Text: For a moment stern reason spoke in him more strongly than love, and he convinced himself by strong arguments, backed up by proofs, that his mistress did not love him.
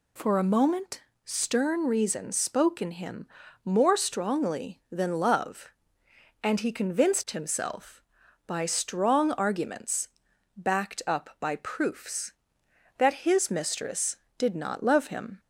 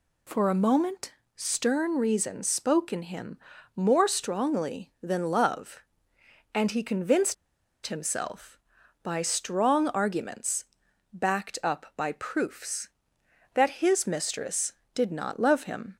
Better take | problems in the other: first | pauses between "moment" and "stern"; slight; at 1.1 s; 0.22 s long; slight in the first // pauses between "him" and "more"; slight; at 3.3 s; 0.36 s long; slight in the first // pauses between "convinced" and "himself"; noticeable; at 7.3 s; 0.51 s long

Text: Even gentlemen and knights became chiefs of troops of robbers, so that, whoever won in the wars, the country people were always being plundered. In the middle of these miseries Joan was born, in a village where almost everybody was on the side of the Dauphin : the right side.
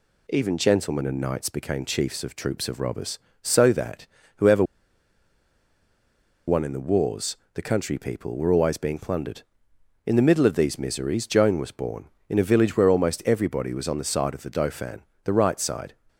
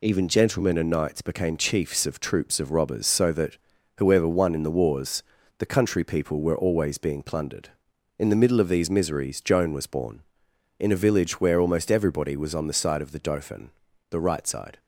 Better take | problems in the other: second | pauses between "whoever" and "won"; strong; at 4.6 s; 1.8 s long

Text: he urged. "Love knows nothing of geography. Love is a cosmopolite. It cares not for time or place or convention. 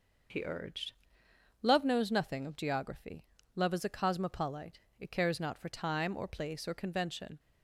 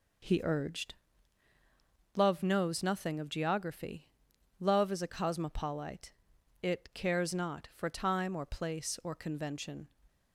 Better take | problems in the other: neither | none

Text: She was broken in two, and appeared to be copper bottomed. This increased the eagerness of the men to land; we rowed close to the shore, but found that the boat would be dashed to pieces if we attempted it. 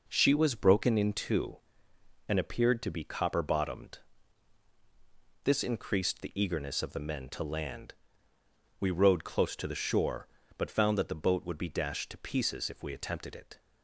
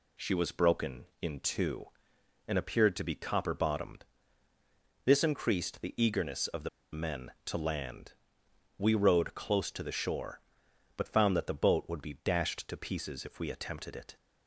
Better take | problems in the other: first | pauses between "the" and "men"; slight; at 6.6 s; 0.25 s long

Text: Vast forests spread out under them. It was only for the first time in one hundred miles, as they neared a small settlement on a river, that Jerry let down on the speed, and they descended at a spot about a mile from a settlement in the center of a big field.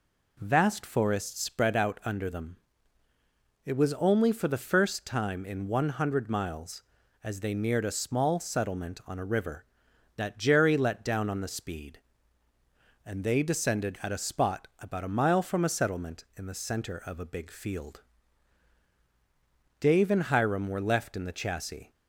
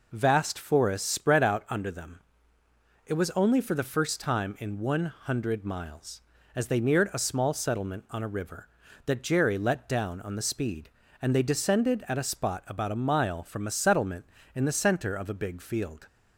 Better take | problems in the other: second | goes on to say "Dave and Hiram were left in the chassis"; strong; from 19.8 s on; 2.1 s long

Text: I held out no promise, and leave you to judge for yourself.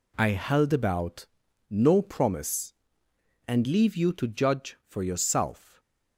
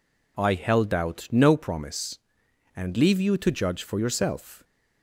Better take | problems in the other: second | says "about" for "out"; at 0.7 s // stays silent after the last word; slight; from 5.5 s on; 0.6 s long

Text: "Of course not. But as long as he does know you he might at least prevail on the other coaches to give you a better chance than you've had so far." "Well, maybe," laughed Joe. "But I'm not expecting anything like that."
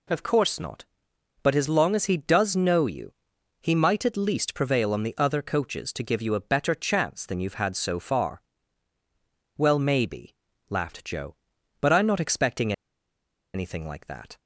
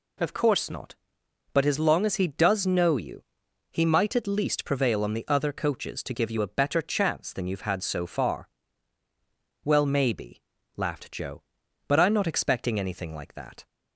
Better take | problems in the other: second | pauses between "you" and "he"; noticeable; at 3.1 s; 0.48 s long; noticeable in the second // pauses between "expecting" and "anything"; noticeable; at 12.7 s; 0.81 s long

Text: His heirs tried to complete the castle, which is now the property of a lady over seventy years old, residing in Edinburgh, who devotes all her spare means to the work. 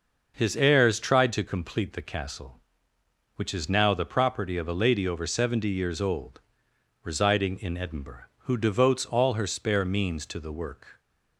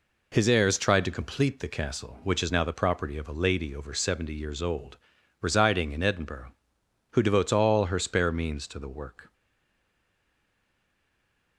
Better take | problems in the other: first | stays silent after the last word; from 9.3 s on; 2.2 s long

